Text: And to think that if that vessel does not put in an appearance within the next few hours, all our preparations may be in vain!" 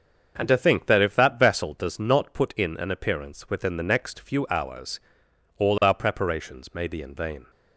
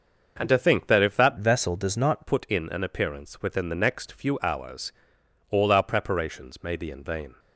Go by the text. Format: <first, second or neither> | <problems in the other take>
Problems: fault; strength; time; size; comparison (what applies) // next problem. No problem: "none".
first | starts louder than the rest; until 1.4 s; 6.5 dB; also in the first // changes voice from "vessel" to "not"; from 1.3 to 2.2 s; 0.9 s long